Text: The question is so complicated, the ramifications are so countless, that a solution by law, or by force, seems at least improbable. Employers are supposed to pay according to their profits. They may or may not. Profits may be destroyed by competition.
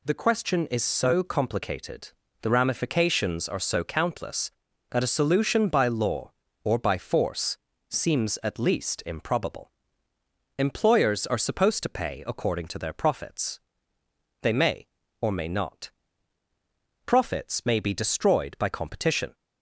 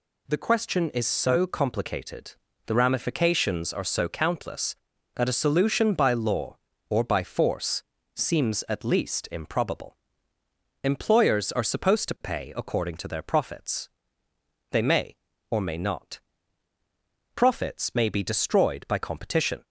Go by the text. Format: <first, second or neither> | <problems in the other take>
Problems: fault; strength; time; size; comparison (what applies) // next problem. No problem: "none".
neither | none